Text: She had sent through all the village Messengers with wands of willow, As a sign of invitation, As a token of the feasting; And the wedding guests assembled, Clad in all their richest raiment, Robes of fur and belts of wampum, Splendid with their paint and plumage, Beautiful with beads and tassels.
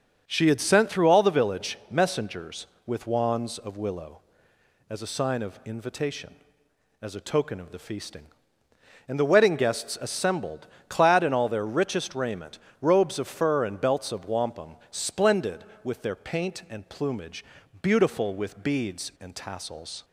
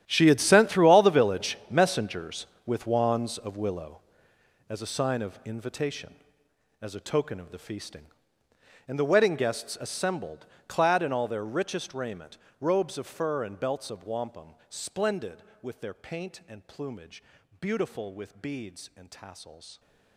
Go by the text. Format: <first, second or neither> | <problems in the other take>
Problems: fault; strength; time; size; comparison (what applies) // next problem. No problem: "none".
first | gets quieter; strong; throughout; 16.5 dB // starts louder than the rest; strong; until 1.0 s; 12 dB; also in the first